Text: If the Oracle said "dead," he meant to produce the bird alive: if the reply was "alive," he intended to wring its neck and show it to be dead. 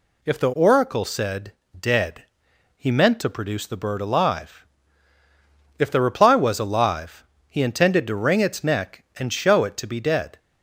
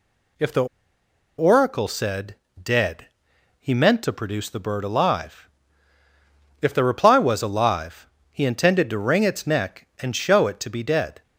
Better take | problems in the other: first | pauses between "the" and "Oracle"; noticeable; at 0.6 s; 0.73 s long // pauses between "said" and "dead"; slight; at 2.3 s; 0.26 s long; slight in the first

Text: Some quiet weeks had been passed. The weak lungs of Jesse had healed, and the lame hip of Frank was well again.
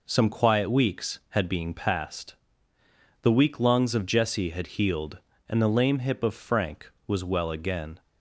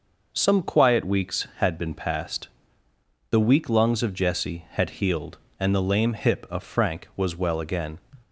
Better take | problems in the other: second | says "being" for "been"; at 1.4 s

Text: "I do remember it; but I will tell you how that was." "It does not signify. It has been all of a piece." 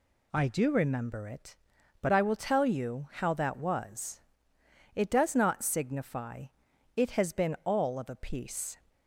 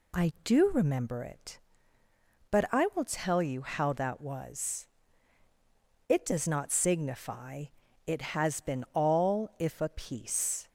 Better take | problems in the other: first | says "if" for "of"; at 9.5 s

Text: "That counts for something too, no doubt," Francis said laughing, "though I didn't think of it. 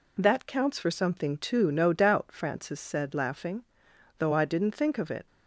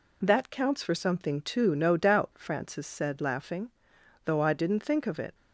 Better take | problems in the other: neither | none

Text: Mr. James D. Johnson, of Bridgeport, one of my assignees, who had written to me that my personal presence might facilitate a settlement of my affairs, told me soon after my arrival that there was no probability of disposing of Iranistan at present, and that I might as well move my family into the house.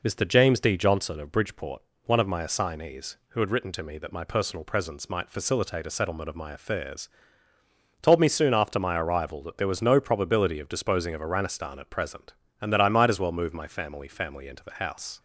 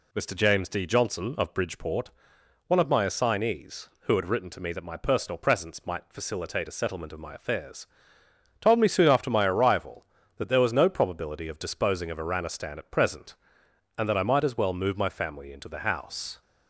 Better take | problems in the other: second | says "family" twice; at 14.0 s

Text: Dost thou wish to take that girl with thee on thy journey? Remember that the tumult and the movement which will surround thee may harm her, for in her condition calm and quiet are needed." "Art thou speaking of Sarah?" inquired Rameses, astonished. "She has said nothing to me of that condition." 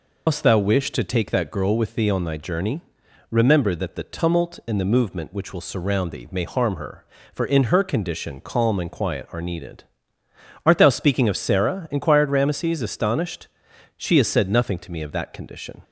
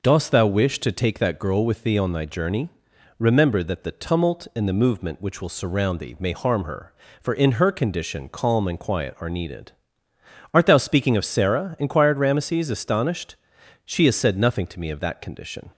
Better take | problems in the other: second | loses the start of "Dost"; at 0.2 s; 125 ms

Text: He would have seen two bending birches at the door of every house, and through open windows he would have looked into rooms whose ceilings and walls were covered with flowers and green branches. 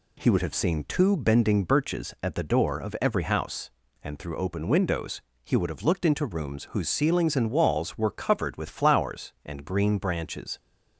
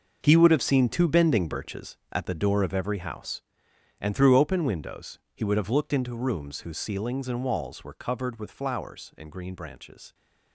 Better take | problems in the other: first | gets quieter; strong; throughout; 12.5 dB // pauses between "windows" and "he"; slight; at 5.1 s; 0.16 s long; slight in the first

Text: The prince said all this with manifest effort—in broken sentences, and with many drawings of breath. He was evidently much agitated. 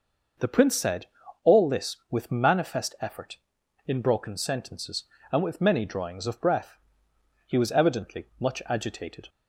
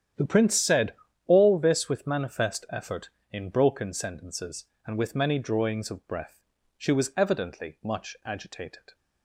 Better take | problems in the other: first | starts louder than the rest; strong; until 1.4 s; 9.5 dB // pauses between "said" and "all"; slight; at 0.9 s; 0.32 s long; slight in the first // says "She" for "He"; at 6.7 s

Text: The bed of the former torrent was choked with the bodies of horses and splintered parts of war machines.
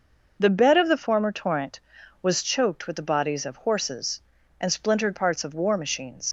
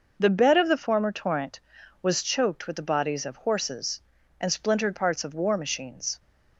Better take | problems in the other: second | leaves "machines" unfinished; at 6.2 s; 85 ms

